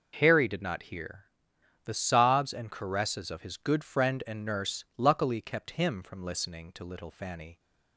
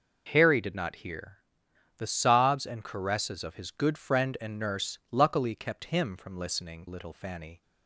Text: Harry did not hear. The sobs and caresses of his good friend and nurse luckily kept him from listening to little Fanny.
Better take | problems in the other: first | skips "to"; at 6.8 s

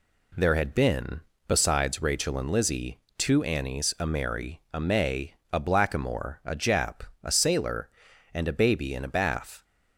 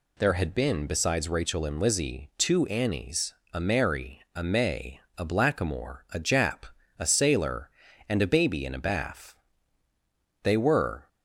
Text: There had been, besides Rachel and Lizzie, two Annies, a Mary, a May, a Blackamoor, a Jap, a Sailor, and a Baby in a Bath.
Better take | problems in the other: first | goes on to say "They were"; noticeable; from 10.4 s on; 0.66 s long

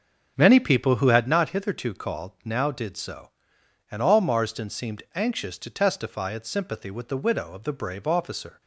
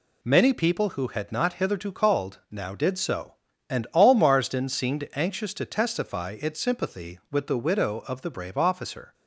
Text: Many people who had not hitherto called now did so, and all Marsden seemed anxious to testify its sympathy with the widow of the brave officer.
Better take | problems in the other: second | starts louder than the rest; until 1.4 s; 7 dB

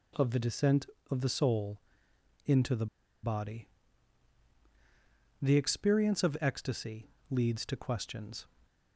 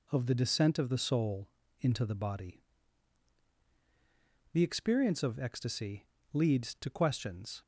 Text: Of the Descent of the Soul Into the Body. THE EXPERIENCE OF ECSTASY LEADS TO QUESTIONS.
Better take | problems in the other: second | pauses between "Soul" and "Into"; noticeable; at 1.8 s; 0.66 s long; slight in the second // pauses between "the" and "Body"; at 2.8 s; 0.37 s long // pauses between "ECSTASY" and "LEADS"; slight; at 7.1 s; 0.18 s long; slight in the second

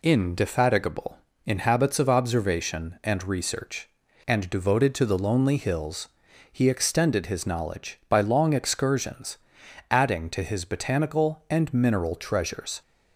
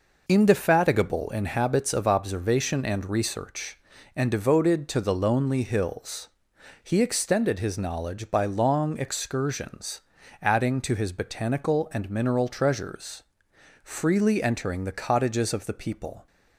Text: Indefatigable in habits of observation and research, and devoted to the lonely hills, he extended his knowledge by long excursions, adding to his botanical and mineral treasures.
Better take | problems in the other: first | goes on to say "Freely entering the cottages of the people"; strong; from 13.8 s on; 2.4 s long

